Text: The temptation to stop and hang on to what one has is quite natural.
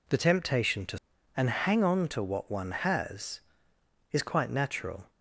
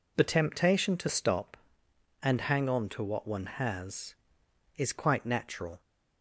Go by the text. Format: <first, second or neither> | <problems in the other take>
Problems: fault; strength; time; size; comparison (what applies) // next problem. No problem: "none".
second | skips "stop"; at 1.1 s